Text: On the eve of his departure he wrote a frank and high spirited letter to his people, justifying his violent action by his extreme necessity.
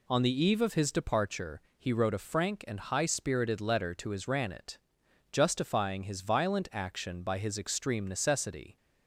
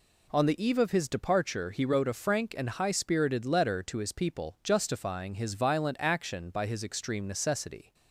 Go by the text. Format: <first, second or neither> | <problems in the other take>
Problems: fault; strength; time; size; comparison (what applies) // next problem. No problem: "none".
second | pauses between "departure" and "he"; slight; at 1.6 s; 0.16 s long // says "ranet" for "people"; at 4.2 s